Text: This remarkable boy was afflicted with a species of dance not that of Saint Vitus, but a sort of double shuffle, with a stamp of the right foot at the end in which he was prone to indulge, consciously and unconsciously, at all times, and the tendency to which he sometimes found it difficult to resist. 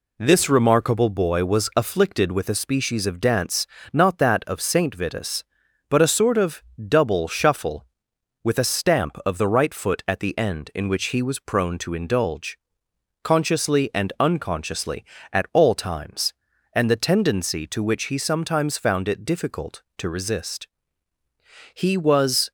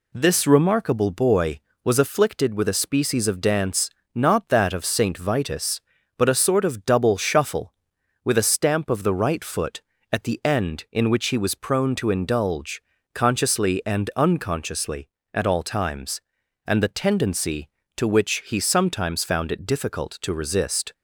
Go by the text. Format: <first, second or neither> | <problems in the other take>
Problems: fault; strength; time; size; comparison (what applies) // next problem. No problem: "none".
second | pauses between "dance" and "not"; slight; at 3.6 s; 0.26 s long; slight in the second // pauses between "of" and "double"; slight; at 6.6 s; 0.24 s long // goes on to say "He was"; noticeable; from 21.7 s on; 0.76 s long